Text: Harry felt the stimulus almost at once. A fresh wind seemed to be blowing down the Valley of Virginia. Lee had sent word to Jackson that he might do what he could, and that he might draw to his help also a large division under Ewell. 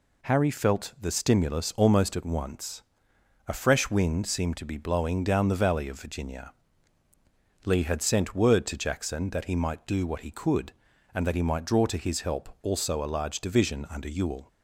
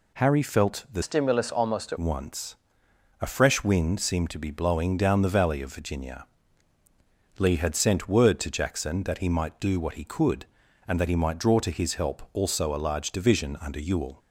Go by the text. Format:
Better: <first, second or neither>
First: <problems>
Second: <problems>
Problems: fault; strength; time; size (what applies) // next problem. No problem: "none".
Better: first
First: none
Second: changes voice from "stimulus" to "at"; from 1.0 to 1.9 s; 0.9 s long